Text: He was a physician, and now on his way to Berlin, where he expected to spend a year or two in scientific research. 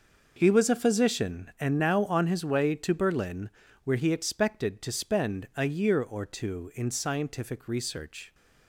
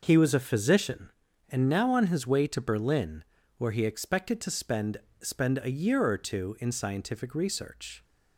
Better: first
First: none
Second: says "spend" twice; at 5.2 s

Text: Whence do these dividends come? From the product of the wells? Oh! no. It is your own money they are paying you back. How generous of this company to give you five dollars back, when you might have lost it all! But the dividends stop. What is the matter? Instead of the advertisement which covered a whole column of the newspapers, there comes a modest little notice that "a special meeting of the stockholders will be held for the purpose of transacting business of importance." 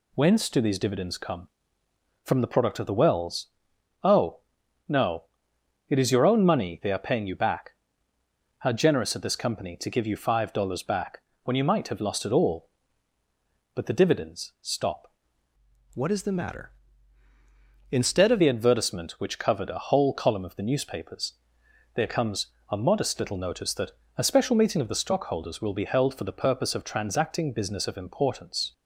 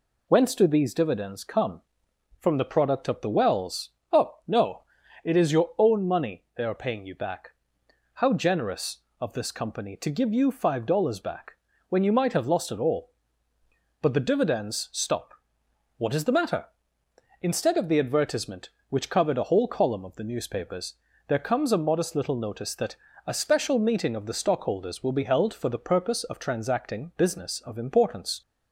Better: second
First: changes voice from "What" to "of"; from 15.9 to 18.4 s; 2.5 s long // pauses between "comes" and "a"; slight; at 22.4 s; 0.24 s long // pauses between "that" and "a"; slight; at 23.9 s; 0.24 s long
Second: pauses between "that" and "a"; slight; at 22.9 s; 0.30 s long

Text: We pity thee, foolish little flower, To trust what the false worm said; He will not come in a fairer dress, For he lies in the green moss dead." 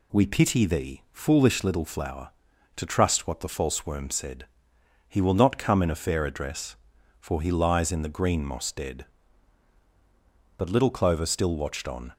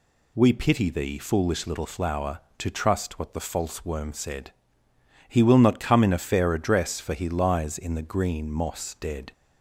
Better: second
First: goes on to say "But little Clover still watched on"; from 10.5 s on; 1.5 s long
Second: none

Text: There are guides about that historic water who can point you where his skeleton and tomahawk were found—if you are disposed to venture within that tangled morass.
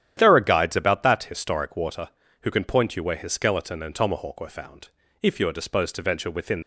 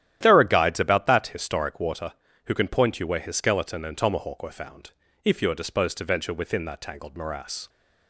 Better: second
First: starts louder than the rest; strong; until 1.1 s; 10.5 dB // stops before "that tangled morass"; at 6.6 s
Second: starts louder than the rest; strong; until 1.2 s; 11.5 dB

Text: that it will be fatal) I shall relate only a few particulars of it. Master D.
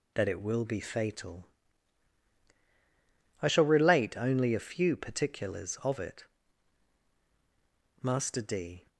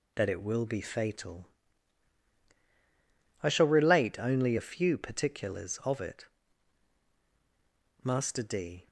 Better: neither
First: none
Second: none

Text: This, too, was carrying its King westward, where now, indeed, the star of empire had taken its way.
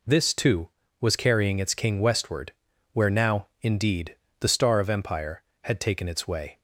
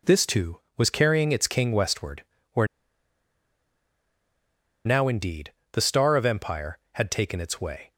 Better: first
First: none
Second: pauses between "where" and "now"; strong; at 2.6 s; 2.1 s long

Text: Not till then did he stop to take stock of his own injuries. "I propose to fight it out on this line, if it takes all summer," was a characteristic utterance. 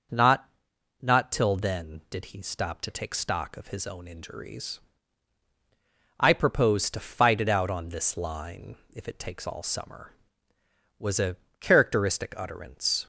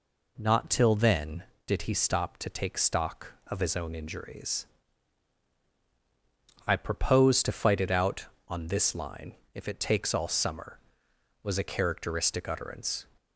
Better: second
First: starts louder than the rest; noticeable; until 1.6 s; 6 dB // says "Not" twice; at 1.0 s // pauses between "a" and "characteristic"; slight; at 11.3 s; 0.24 s long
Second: none

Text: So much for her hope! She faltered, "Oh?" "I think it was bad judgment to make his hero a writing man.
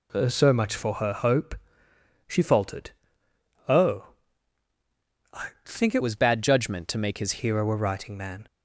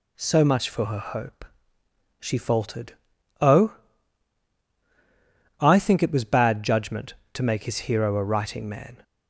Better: second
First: changes voice from "was" to "his"; from 6.0 to 7.4 s; 1.4 s long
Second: none

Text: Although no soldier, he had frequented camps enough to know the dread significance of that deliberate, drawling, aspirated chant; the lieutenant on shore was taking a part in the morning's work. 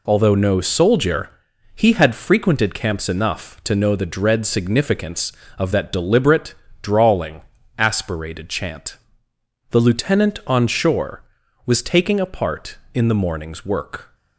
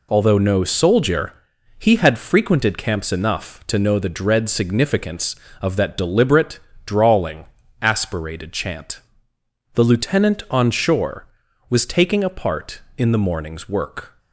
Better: neither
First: none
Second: none

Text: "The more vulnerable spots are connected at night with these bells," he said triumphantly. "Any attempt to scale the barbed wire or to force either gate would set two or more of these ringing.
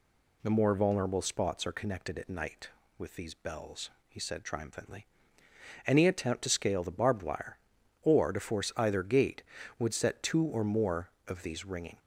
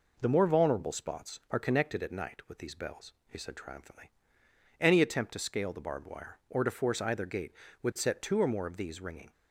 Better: neither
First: none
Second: none

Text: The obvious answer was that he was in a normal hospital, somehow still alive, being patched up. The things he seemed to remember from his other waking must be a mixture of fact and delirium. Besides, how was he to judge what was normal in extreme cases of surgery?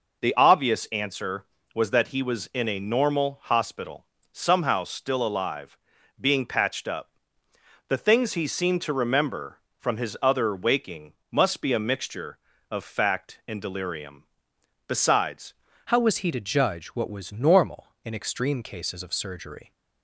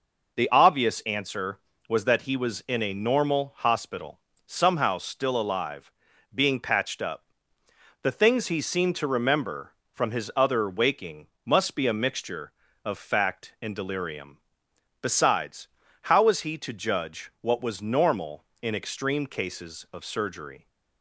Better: second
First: pauses between "waking" and "must"; slight; at 11.1 s; 0.16 s long // changes voice at "how"; from 15.8 s on; 3.9 s long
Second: pauses between "waking" and "must"; slight; at 11.2 s; 0.16 s long

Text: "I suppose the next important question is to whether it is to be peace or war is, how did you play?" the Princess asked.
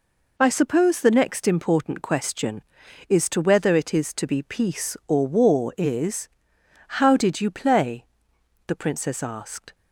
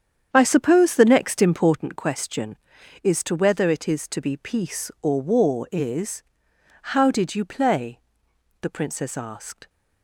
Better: first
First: none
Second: starts louder than the rest; strong; until 1.9 s; 8.5 dB

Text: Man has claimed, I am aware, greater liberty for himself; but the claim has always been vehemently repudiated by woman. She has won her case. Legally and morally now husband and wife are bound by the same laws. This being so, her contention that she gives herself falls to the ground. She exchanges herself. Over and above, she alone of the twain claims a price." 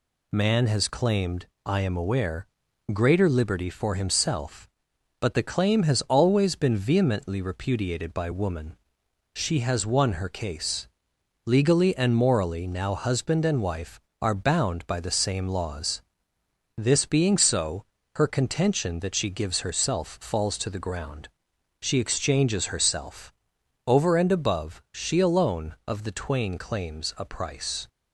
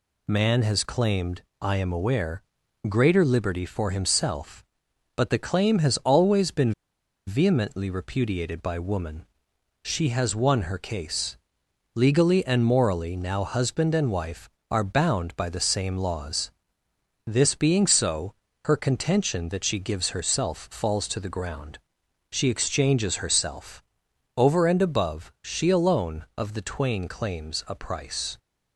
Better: first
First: none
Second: pauses between "been" and "vehemently"; noticeable; at 6.7 s; 0.55 s long

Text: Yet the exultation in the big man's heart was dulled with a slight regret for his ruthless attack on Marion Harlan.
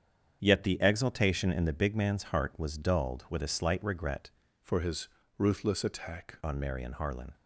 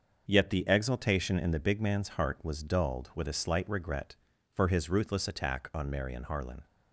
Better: second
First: starts louder than the rest; strong; until 1.4 s; 8 dB // changes voice from "for" to "attack"; from 4.6 to 6.3 s; 1.7 s long // pauses between "his" and "ruthless"; slight; at 5.0 s; 0.28 s long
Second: starts louder than the rest; until 1.3 s; 6.5 dB

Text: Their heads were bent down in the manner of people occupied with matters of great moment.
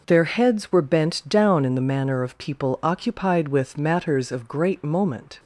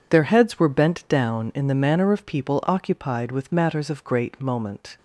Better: neither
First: none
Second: none

